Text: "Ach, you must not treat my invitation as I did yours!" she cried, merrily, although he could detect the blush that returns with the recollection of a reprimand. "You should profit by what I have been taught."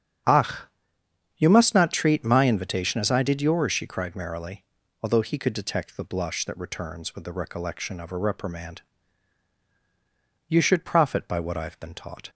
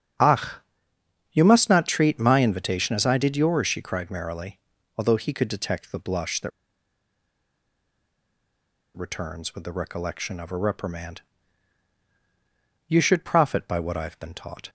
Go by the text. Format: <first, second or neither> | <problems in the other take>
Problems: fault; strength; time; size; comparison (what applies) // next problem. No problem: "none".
first | starts louder than the rest; strong; until 2.1 s; 8 dB; strong in the first // pauses between "that" and "returns"; strong; at 6.5 s; 2.4 s long